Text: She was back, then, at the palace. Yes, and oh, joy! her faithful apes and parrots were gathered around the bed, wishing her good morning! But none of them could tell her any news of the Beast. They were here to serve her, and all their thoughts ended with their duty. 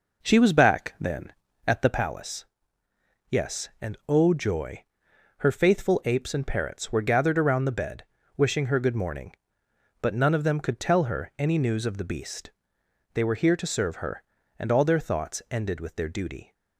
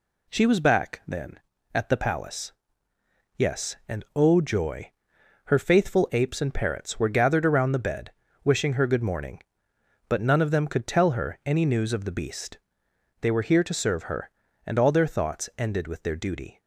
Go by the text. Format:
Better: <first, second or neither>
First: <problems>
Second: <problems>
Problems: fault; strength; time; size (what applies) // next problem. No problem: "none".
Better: second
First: starts louder than the rest; noticeable; until 2.1 s; 4.5 dB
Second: none